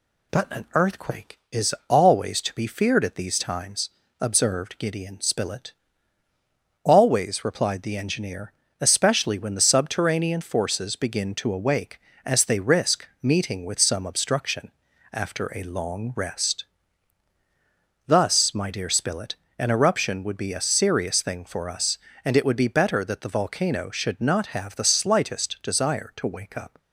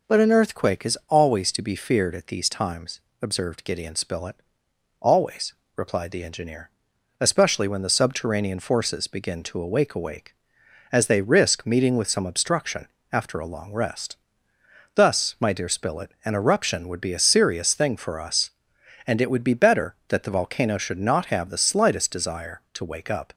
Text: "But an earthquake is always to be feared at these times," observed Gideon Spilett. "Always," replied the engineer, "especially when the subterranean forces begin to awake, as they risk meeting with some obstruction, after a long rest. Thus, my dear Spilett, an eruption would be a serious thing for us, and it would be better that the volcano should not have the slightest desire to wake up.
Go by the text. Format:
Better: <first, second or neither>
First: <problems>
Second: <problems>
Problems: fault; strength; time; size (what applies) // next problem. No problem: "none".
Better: first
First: none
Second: says "awake" twice; at 9.9 s